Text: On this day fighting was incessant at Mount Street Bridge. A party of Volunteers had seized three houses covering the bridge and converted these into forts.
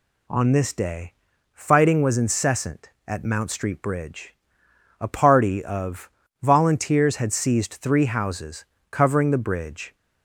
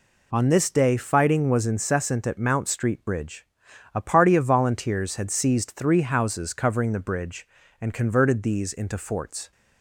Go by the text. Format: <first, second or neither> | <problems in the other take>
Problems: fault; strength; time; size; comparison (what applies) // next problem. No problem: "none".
second | pauses between "day" and "fighting"; at 1.1 s; 0.40 s long // pauses between "of" and "Volunteers"; slight; at 6.1 s; 0.32 s long // pauses between "houses" and "covering"; slight; at 8.6 s; 0.26 s long // stops before "and converted these into forts"; at 9.9 s